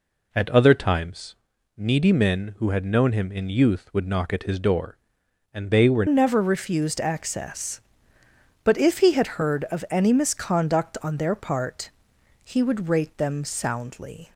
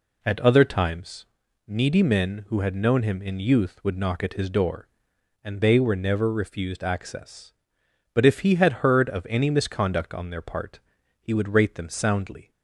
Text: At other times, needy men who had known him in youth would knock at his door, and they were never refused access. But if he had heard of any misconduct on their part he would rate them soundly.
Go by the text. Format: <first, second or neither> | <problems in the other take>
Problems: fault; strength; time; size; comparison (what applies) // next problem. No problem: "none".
second | changes voice at "never"; from 6.0 s on; 8.3 s long // pauses between "part" and "he"; noticeable; at 11.9 s; 0.54 s long; also in the second